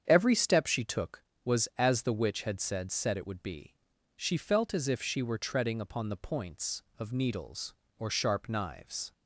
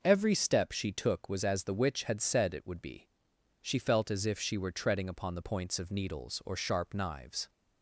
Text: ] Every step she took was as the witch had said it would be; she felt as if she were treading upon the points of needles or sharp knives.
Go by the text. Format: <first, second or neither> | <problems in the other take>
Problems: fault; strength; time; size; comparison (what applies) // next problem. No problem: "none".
second | starts louder than the rest; strong; until 1.0 s; 8 dB // says "said" twice; at 2.9 s